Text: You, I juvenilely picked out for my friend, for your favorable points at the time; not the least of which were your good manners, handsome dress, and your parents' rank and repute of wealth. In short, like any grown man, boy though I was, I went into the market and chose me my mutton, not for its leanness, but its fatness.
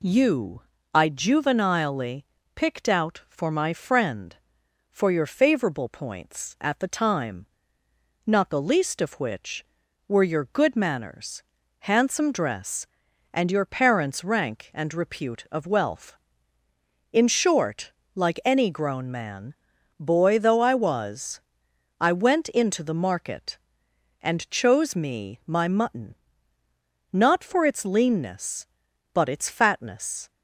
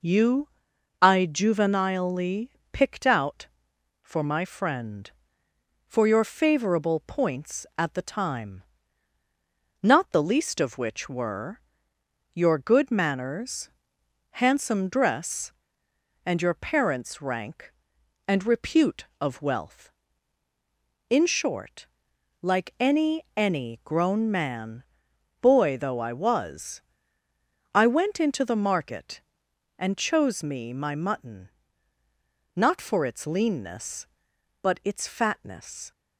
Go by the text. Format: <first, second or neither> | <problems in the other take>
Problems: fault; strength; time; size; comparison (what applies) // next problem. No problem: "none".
first | pauses between "juvenilely" and "picked"; slight; at 2.4 s; 0.24 s long; slight in the first // pauses between "were" and "your"; noticeable; at 11.6 s; 0.72 s long // says "any" twice; at 23.3 s